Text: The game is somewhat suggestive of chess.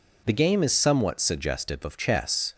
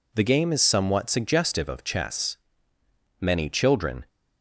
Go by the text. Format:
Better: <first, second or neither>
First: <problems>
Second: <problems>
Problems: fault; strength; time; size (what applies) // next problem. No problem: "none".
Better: first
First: none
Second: goes on to say "Many children"; noticeable; from 3.1 s on; 0.88 s long